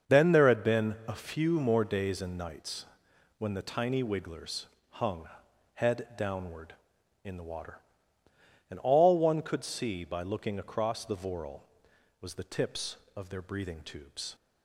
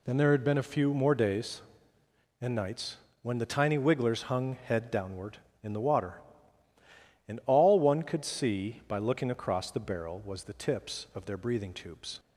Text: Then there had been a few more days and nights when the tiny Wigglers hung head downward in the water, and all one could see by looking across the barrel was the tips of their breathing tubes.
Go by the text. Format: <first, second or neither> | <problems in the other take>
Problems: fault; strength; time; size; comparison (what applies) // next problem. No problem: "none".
second | starts louder than the rest; until 1.1 s; 6.5 dB // pauses between "nights" and "when"; noticeable; at 2.8 s; 0.54 s long; slight in the second // pauses between "Wigglers" and "hung"; slight; at 4.6 s; 0.24 s long // pauses between "hung" and "head"; noticeable; at 5.2 s; 0.48 s long // says "voral" for "barrel"; at 11.1 s